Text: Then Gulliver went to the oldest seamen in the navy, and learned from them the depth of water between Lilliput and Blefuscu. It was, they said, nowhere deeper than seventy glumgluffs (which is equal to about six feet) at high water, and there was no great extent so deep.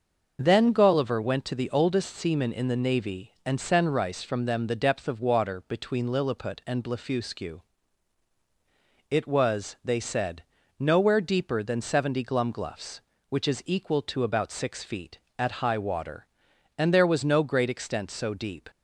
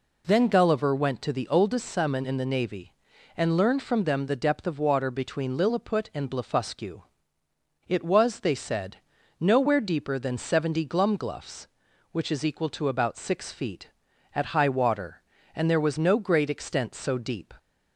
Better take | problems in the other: second | starts louder than the rest; until 1.4 s; 6.5 dB // says "senrice" for "learned"; at 3.5 s

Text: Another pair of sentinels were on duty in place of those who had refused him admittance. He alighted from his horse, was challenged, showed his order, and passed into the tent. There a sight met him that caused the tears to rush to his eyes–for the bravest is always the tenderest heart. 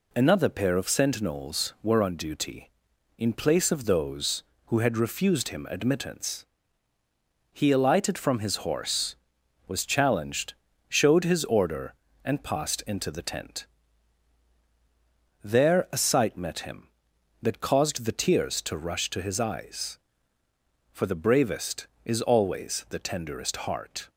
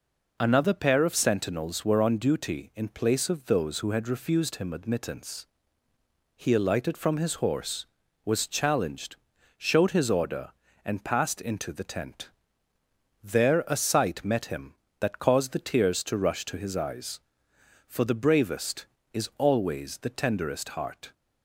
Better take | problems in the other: neither | none

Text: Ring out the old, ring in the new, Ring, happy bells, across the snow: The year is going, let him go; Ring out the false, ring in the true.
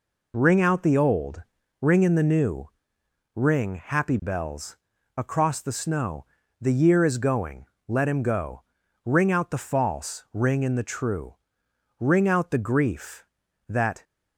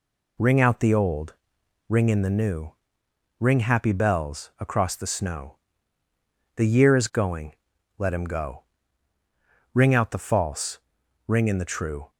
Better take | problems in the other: second | goes on to say "Ring out the grief that"; strong; from 11.9 s on; 2.0 s long

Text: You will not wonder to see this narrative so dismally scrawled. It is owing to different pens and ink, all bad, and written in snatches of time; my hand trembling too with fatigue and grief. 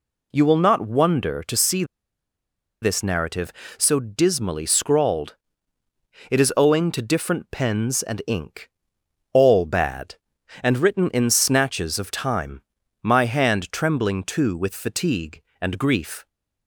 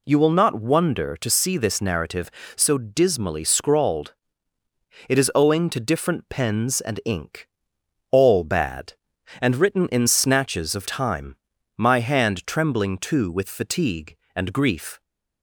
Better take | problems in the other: second | pauses between "see" and "this"; noticeable; at 1.8 s; 0.97 s long

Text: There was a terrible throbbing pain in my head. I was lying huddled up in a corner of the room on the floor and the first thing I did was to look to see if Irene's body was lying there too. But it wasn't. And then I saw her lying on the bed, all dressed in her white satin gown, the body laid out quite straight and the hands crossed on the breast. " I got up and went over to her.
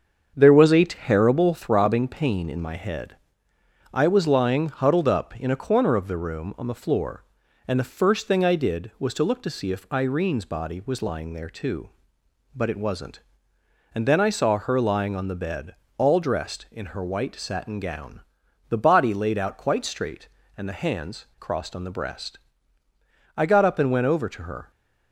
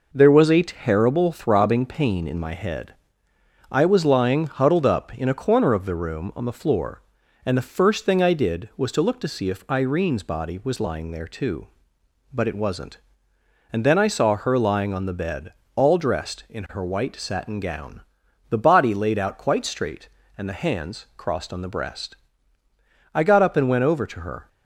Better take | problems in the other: second | starts louder than the rest; until 1.8 s; 7 dB

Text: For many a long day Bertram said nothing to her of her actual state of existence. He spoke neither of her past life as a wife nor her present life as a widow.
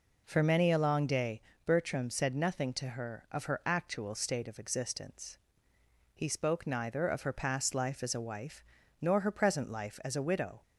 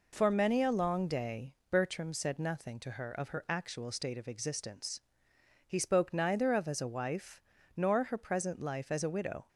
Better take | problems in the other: first | pauses between "day" and "Bertram"; slight; at 1.5 s; 0.16 s long; slight in the first // skips "her past life"; at 6.6 s // pauses between "wife" and "nor"; slight; at 7.4 s; 0.34 s long; slight in the first

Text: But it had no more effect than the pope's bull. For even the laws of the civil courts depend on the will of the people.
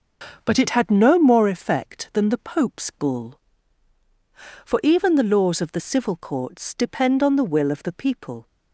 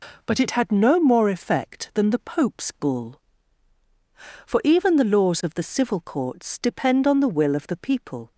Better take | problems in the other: second | starts louder than the rest; noticeable; until 1.5 s; 6 dB

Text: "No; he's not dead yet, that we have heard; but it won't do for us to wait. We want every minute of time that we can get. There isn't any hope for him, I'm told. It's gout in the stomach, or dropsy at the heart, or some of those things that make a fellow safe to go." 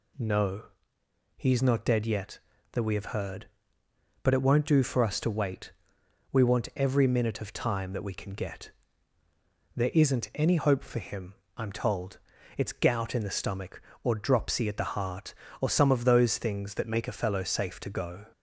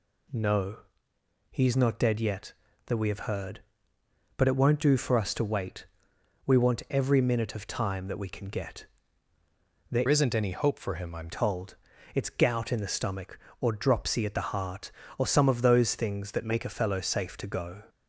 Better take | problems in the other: first | changes voice from "isn't" to "I'm"; from 10.0 to 11.2 s; 1.2 s long

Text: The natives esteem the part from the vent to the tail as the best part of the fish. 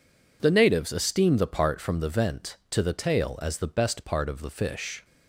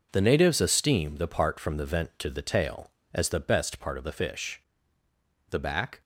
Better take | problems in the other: first | goes on to say "The back"; from 5.5 s on; 0.50 s long

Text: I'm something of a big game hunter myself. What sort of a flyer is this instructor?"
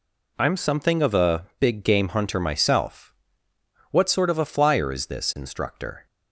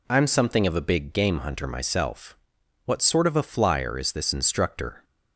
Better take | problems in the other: neither | none

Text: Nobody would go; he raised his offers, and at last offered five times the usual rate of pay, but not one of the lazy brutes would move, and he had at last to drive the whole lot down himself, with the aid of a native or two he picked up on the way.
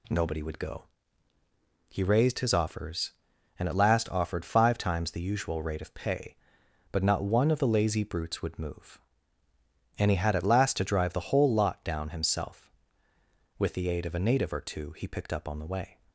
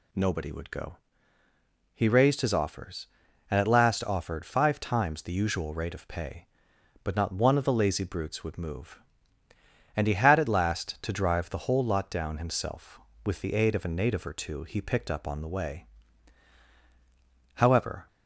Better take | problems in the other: first | goes on to say "However"; from 17.5 s on; 0.52 s long

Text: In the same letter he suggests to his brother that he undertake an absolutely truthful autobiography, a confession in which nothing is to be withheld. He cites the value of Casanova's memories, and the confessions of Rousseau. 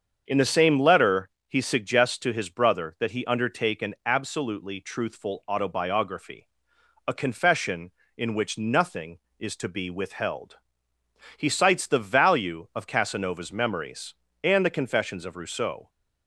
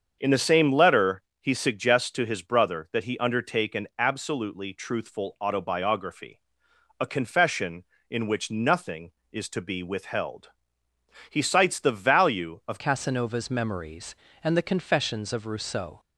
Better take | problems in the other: first | starts louder than the rest; until 1.2 s; 7 dB; also in the first // pauses between "letter" and "he"; slight; at 1.2 s; 0.20 s long; slight in the first // changes voice at "Casanova's"; from 12.7 s on; 3.2 s long

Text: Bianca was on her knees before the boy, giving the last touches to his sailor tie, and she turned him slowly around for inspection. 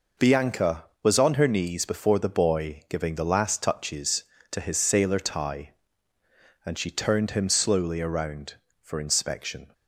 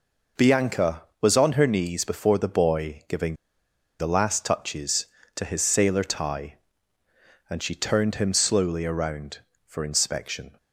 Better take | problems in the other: first | pauses between "giving" and "the"; noticeable; at 3.3 s; 0.64 s long

